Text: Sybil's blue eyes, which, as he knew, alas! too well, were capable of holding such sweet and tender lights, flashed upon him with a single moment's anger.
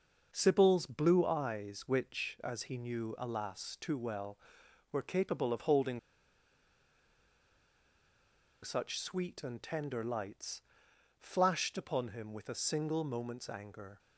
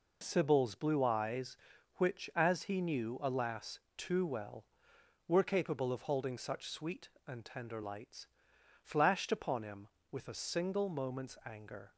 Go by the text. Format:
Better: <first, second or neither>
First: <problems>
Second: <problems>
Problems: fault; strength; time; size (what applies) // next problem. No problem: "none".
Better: second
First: pauses between "holding" and "such"; strong; at 5.9 s; 2.6 s long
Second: none